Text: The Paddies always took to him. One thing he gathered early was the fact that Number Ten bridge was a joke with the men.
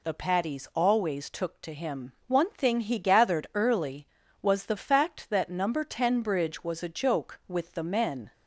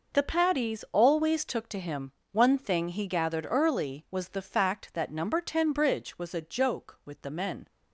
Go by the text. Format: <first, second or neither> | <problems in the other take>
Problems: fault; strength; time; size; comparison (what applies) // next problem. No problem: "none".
neither | none